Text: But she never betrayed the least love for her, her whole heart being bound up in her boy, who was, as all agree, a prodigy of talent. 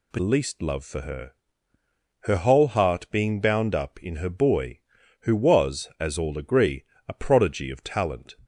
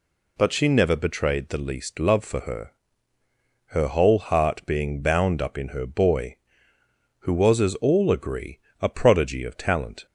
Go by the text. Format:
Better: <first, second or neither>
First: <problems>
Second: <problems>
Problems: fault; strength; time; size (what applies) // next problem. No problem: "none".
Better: second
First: skips "she never betrayed the"; at 0.1 s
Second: none